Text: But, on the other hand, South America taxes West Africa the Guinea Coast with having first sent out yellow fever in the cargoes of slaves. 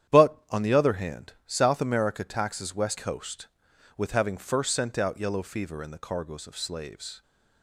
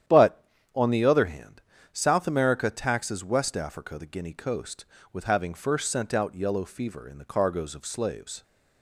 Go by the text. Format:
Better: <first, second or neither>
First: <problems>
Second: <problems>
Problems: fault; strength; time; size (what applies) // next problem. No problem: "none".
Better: second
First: starts louder than the rest; strong; until 1.2 s; 10 dB // skips "Africa the Guinea"; at 2.9 s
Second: starts louder than the rest; strong; until 1.3 s; 10 dB